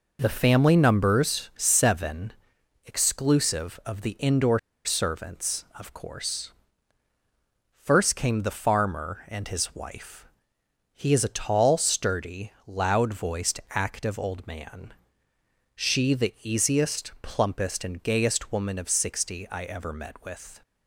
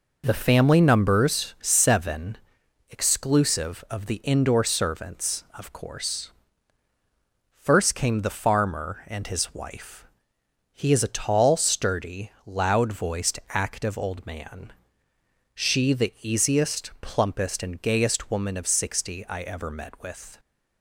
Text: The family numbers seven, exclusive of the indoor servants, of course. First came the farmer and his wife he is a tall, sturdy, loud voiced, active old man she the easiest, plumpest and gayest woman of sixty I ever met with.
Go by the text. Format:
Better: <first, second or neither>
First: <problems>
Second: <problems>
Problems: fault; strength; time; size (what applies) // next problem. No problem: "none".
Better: second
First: pauses between "indoor" and "servants"; slight; at 4.5 s; 0.26 s long // pauses between "wife" and "he"; noticeable; at 10.2 s; 0.66 s long // pauses between "man" and "she"; noticeable; at 14.9 s; 0.80 s long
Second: pauses between "wife" and "he"; noticeable; at 10.0 s; 0.66 s long // pauses between "man" and "she"; noticeable; at 14.7 s; 0.80 s long